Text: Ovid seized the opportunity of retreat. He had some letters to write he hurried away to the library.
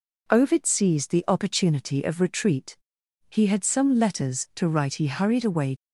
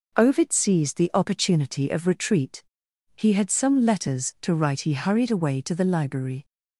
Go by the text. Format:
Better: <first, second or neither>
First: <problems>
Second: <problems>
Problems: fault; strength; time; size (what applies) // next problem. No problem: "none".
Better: second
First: stops before "to the library"; at 5.7 s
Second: none